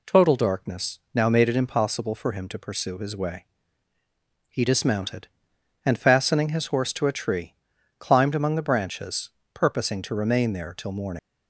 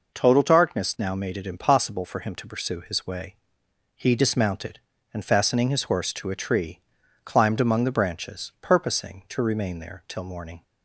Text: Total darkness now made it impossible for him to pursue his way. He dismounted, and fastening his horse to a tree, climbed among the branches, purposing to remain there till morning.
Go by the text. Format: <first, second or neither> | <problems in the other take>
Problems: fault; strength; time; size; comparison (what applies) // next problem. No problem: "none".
second | leaves "morning" unfinished; at 11.1 s; 80 ms